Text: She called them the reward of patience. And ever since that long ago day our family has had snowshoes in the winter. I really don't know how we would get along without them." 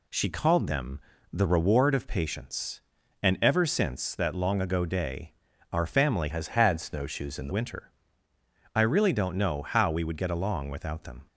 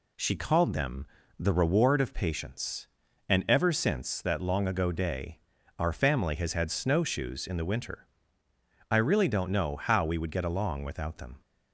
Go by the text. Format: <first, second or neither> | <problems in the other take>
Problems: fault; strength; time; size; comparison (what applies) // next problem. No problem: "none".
second | pauses between "them" and "the"; slight; at 0.9 s; 0.32 s long; slight in the second // pauses between "day" and "our"; at 5.3 s; 0.38 s long; also in the second // changes voice from "has" to "the"; from 6.3 to 7.5 s; 1.2 s long